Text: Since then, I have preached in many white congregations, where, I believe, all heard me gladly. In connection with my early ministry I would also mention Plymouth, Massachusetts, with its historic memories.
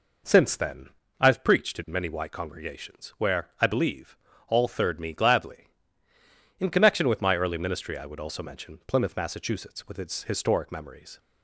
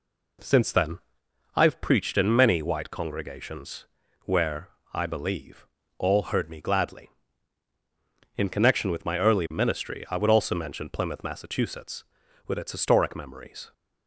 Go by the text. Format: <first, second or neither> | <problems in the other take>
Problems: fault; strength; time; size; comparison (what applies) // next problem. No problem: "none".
second | says "third" for "heard"; at 4.6 s